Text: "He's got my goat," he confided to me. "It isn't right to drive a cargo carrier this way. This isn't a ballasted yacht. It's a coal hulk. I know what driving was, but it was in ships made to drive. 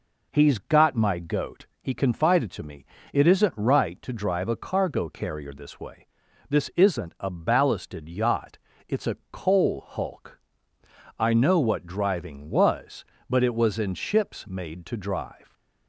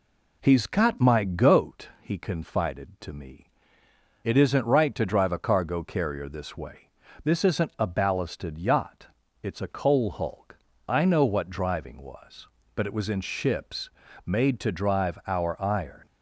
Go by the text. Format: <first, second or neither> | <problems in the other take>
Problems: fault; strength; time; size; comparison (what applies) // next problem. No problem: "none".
first | pauses between "ships" and "made"; slight; at 13.8 s; 0.36 s long // goes on to say "Our iron"; noticeable; from 15.2 s on; 0.78 s long